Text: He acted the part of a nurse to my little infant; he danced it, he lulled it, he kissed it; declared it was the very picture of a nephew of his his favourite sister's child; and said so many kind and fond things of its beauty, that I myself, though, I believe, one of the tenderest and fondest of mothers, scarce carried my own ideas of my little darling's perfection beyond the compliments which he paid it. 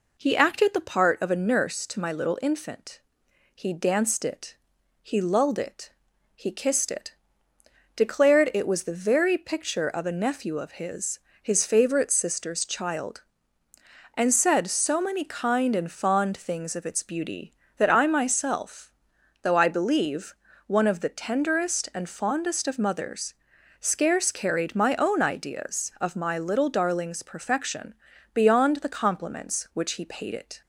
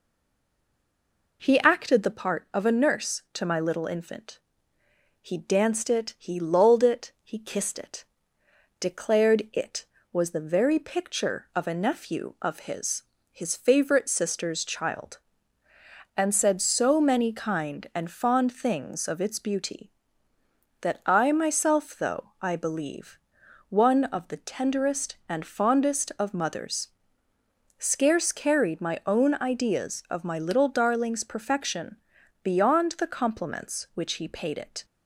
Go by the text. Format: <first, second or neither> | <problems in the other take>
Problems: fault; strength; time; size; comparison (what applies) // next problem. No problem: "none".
first | stays silent before the first word; noticeable; until 1.4 s; 1.4 s long // pauses between "his" and "his"; slight; at 13.0 s; 0.30 s long; slight in the first // pauses between "perfection" and "beyond"; noticeable; at 31.9 s; 0.46 s long; also in the first